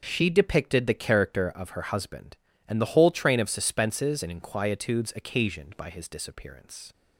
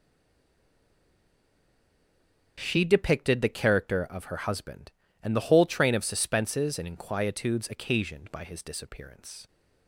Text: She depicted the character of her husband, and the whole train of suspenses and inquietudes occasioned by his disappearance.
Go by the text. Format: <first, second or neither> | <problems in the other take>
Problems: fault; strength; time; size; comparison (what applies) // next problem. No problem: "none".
first | stays silent before the first word; strong; until 2.5 s; 2.5 s long // starts louder than the rest; noticeable; until 3.6 s; 6 dB; noticeable in the first